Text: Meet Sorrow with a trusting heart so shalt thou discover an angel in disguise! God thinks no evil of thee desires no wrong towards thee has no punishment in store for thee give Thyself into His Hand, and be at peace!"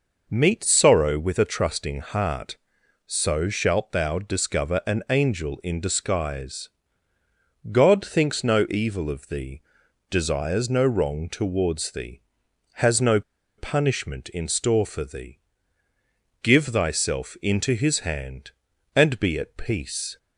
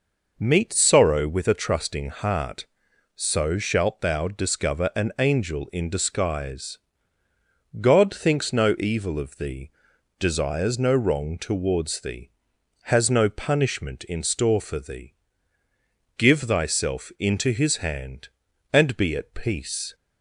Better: second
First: pauses between "thee" and "desires"; noticeable; at 9.6 s; 0.48 s long // pauses between "no" and "punishment"; at 13.2 s; 0.36 s long // pauses between "thee" and "give"; at 15.3 s; 1.0 s long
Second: pauses between "thee" and "desires"; noticeable; at 9.7 s; 0.48 s long // pauses between "thee" and "give"; at 15.1 s; 1.0 s long

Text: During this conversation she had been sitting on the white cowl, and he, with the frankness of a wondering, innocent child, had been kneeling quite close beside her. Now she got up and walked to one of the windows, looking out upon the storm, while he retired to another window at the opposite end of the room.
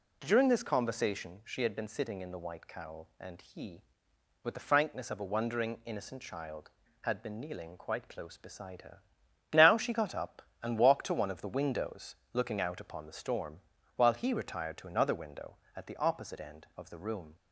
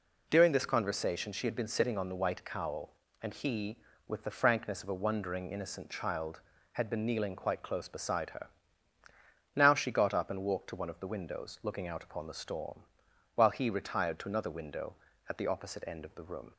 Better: second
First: says "in" for "on"; at 2.2 s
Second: none

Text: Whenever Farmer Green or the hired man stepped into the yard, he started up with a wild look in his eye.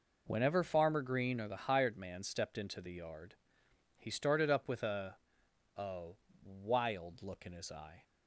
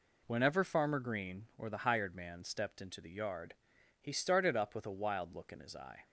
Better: second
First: says "a" twice; at 5.7 s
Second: none

